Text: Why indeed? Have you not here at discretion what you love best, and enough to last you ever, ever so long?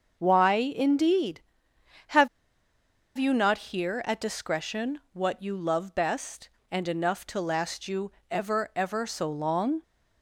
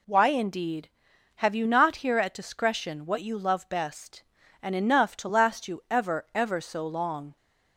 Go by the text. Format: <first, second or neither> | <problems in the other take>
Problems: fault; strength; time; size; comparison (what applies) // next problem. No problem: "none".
second | starts louder than the rest; until 1.1 s; 6.5 dB // pauses between "Have" and "you"; noticeable; at 2.2 s; 0.89 s long // pauses between "you" and "ever"; slight; at 8.1 s; 0.20 s long